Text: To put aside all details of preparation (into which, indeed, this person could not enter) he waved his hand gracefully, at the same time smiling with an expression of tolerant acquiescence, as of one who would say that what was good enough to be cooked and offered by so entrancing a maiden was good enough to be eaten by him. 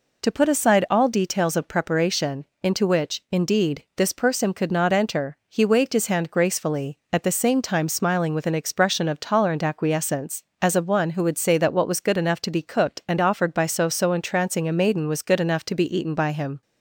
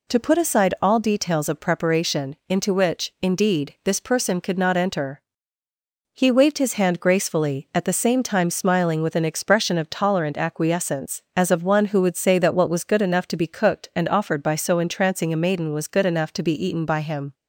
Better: second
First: says "so" twice; at 13.8 s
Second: none

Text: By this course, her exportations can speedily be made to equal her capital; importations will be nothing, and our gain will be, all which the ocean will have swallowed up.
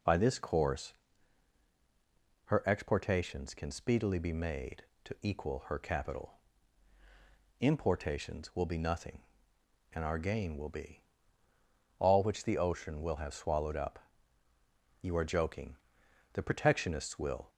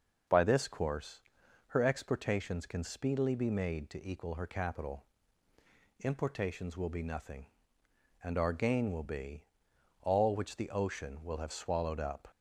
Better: second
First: goes on to say "You are joking the protectionists will"; strong; from 15.0 s on; 2.4 s long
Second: none

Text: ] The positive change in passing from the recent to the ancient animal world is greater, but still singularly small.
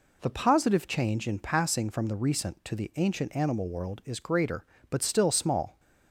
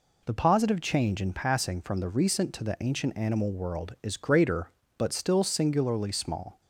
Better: second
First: skips "singularly"; at 5.3 s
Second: none

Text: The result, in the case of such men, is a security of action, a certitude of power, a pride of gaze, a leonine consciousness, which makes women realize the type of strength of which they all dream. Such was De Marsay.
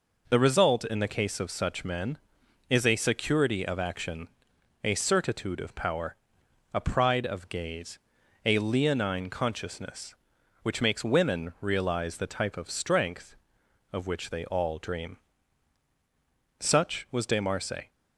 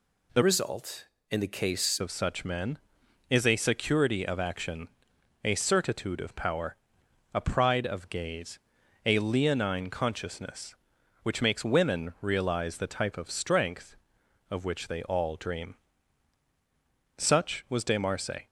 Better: first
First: none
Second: changes voice from "result" to "case"; from 0.4 to 1.9 s; 1.5 s long

